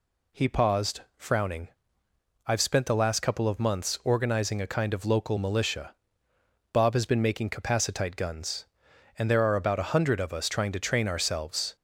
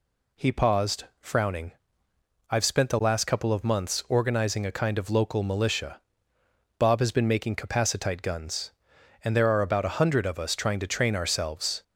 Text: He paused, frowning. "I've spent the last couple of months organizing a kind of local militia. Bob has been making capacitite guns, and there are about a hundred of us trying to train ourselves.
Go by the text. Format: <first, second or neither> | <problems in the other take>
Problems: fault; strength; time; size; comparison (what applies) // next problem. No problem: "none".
neither | none